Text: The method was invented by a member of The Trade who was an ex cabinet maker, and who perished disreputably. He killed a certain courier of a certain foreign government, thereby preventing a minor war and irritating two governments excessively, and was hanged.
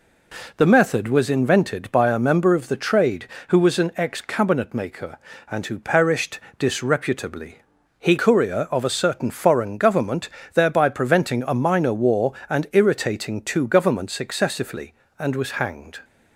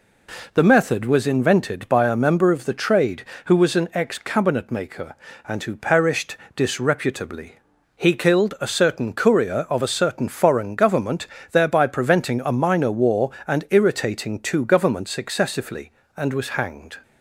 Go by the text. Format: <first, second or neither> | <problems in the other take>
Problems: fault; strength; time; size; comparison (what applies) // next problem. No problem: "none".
second | pauses between "perished" and "disreputably"; slight; at 6.4 s; 0.16 s long; slight in the second // skips "killed a certain"; at 8.1 s